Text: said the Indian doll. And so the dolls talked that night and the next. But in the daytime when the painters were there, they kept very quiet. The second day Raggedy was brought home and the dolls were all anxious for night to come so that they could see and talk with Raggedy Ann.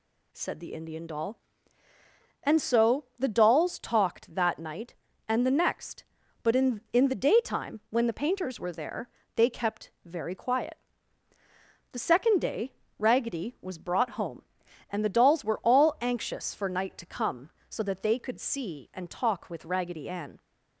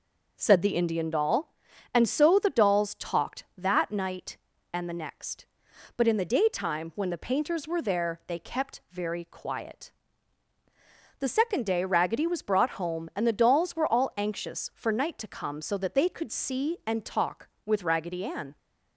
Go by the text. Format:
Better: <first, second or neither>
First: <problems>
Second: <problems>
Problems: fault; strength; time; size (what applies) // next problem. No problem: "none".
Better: second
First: says "in" twice; at 6.9 s // pauses between "day" and "Raggedy"; slight; at 12.7 s; 0.26 s long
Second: none